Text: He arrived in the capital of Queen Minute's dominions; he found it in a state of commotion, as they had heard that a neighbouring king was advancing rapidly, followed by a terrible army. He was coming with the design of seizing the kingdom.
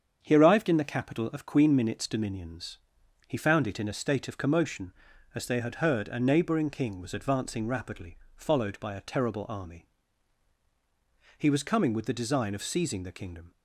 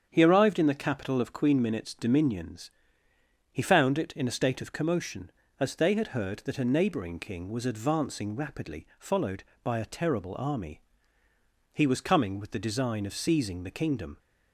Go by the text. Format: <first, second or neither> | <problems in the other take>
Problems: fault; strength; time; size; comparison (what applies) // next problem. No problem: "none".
second | starts louder than the rest; strong; until 1.2 s; 7.5 dB; strong in the second // skips "that"; at 6.0 s